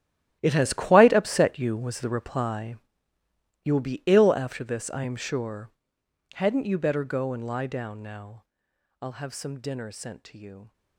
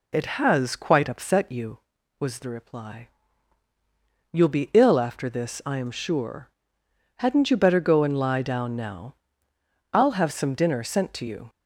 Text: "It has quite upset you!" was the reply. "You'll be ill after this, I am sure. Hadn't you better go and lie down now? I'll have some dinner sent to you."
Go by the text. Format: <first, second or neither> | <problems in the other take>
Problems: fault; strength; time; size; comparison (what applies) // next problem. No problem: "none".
second | gets quieter; strong; throughout; 15.5 dB